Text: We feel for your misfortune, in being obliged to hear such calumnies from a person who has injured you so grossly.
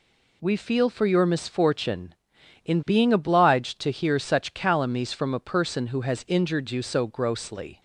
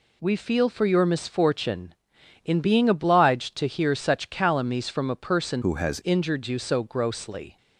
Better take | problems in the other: first | changes voice from "who" to "has"; from 5.6 to 5.9 s; 0.3 s long

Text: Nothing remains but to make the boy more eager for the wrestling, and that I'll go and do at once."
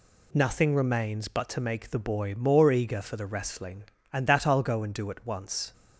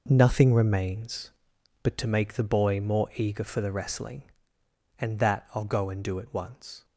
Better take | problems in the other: first | gets quieter; strong; throughout; 10 dB

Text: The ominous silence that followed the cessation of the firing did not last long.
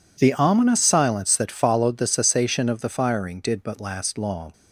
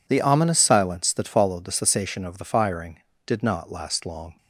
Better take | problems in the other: second | says "but" for "not"; at 3.6 s

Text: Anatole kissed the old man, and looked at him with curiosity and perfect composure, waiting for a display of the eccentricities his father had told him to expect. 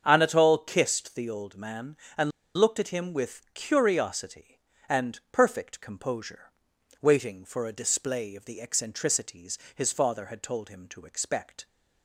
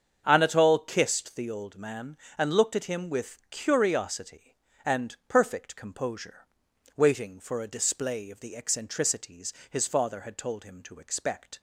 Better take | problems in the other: second | starts louder than the rest; strong; until 1.0 s; 7.5 dB; strong in the second // pauses between "and" and "looked"; slight; at 2.3 s; 0.25 s long // pauses between "eccentricities" and "his"; slight; at 9.5 s; 0.18 s long; slight in the second

